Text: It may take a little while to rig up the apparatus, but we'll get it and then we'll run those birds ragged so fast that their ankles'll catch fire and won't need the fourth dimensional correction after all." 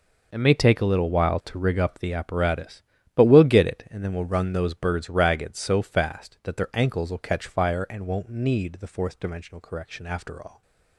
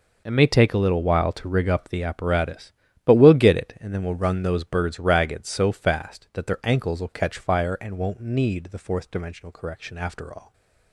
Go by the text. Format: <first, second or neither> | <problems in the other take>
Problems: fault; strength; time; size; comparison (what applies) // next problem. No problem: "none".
neither | stays silent after the last word; slight; the same in both